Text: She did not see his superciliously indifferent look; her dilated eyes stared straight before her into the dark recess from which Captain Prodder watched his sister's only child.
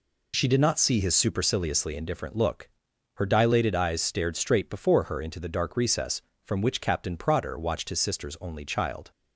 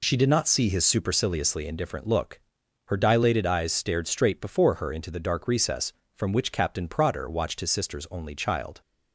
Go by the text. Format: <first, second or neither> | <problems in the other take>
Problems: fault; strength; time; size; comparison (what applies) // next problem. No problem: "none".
neither | none